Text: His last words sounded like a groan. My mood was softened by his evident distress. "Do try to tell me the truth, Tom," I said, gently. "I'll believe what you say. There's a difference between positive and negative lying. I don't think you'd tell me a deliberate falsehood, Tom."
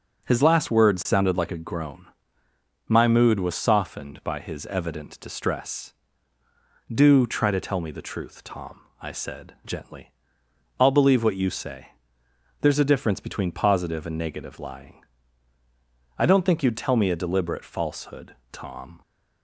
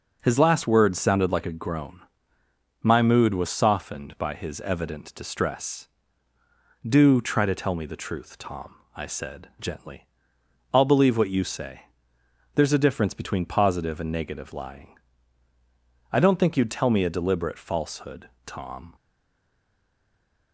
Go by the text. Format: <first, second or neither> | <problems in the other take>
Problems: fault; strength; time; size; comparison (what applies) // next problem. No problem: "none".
first | stays silent after the last word; noticeable; from 18.9 s on; 1.6 s long